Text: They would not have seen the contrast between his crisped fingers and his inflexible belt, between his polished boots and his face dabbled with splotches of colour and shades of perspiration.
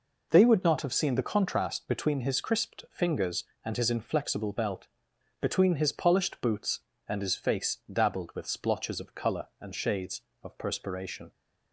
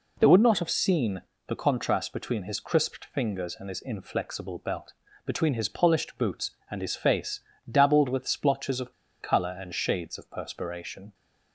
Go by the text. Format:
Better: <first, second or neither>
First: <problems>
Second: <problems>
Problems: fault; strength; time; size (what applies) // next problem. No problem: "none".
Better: first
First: none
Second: pauses between "seen" and "the"; slight; at 1.2 s; 0.26 s long // pauses between "face" and "dabbled"; slight; at 7.4 s; 0.30 s long // pauses between "of" and "colour"; slight; at 8.9 s; 0.28 s long